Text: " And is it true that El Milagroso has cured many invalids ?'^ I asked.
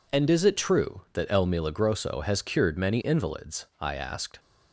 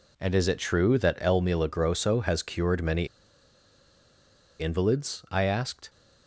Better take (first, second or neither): first